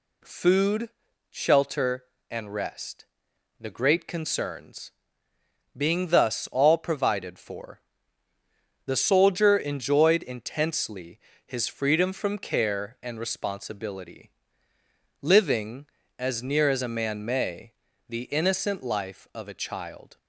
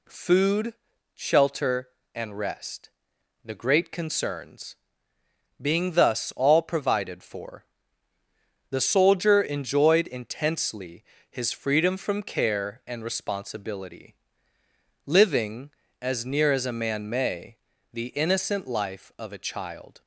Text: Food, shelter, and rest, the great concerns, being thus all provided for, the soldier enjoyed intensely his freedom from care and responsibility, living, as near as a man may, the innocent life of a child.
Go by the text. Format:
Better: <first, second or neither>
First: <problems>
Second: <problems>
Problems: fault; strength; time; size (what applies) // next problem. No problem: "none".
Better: neither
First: pauses between "intensely" and "his"; slight; at 11.1 s; 0.26 s long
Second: pauses between "intensely" and "his"; slight; at 11.0 s; 0.26 s long